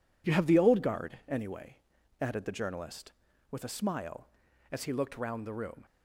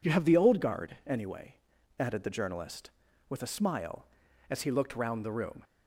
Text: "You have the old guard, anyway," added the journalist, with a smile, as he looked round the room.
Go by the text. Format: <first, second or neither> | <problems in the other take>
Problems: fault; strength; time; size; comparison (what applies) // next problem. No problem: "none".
second | gets quieter; strong; throughout; 8 dB